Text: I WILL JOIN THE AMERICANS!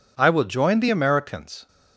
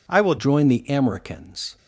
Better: first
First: none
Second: changes voice at "JOIN"; from 0.3 s on; 1.4 s long

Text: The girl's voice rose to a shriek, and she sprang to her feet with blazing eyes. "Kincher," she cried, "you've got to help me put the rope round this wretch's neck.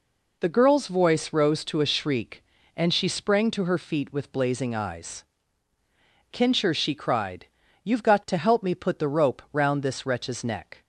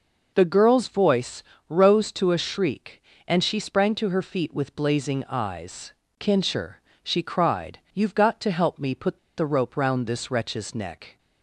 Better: first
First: none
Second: pauses between "voice" and "rose"; slight; at 1.4 s; 0.28 s long // pauses between "put" and "the"; slight; at 9.1 s; 0.20 s long

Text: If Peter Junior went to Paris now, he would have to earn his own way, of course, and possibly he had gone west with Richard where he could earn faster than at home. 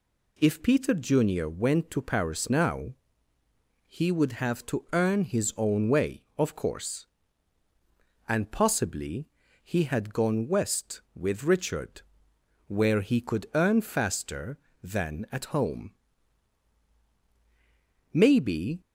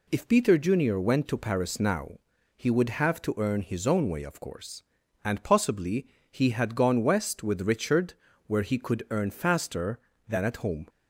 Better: second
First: pauses between "possibly" and "he"; slight; at 9.2 s; 0.36 s long // pauses between "Richard" and "where"; noticeable; at 12.0 s; 0.66 s long // goes on to say "Maybe"; noticeable; from 18.1 s on; 0.68 s long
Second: pauses between "possibly" and "he"; slight; at 6.0 s; 0.24 s long // pauses between "Richard" and "where"; slight; at 8.1 s; 0.32 s long

